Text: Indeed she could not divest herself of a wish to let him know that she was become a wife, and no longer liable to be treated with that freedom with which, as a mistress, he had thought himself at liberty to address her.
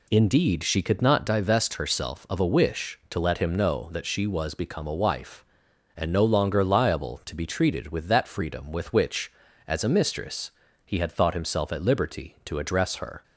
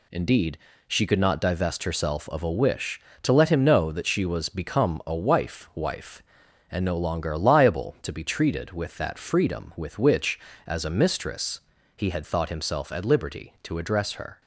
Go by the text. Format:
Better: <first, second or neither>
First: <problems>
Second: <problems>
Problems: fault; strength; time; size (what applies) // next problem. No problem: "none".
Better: first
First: none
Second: pauses between "Indeed" and "she"; slight; at 0.5 s; 0.30 s long // says "wife" twice; at 5.7 s